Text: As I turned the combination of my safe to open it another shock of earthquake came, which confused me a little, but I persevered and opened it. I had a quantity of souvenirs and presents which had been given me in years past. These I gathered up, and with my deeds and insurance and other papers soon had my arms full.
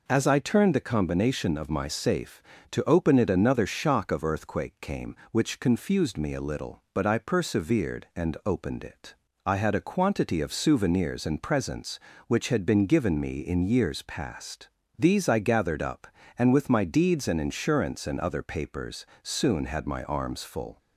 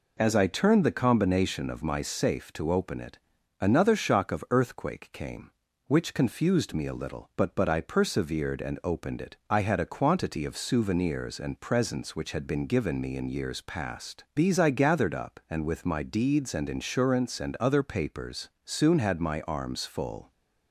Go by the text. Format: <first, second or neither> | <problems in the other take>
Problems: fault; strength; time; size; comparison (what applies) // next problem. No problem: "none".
first | pauses between "it" and "another"; at 3.1 s; 0.42 s long // says "but" twice; at 7.5 s // pauses between "papers" and "soon"; slight; at 18.4 s; 0.16 s long; slight in the first